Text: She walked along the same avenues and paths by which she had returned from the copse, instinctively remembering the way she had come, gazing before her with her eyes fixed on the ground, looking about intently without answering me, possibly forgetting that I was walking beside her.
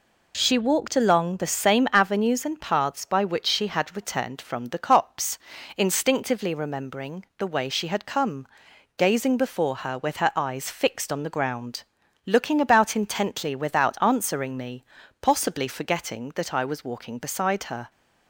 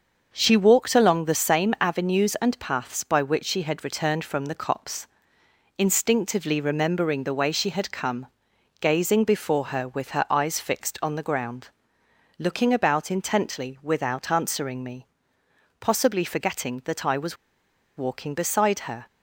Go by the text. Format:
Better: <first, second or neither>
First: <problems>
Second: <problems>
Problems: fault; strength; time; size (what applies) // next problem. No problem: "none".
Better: first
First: none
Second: starts louder than the rest; until 1.3 s; 6.5 dB // pauses between "was" and "walking"; noticeable; at 17.3 s; 0.61 s long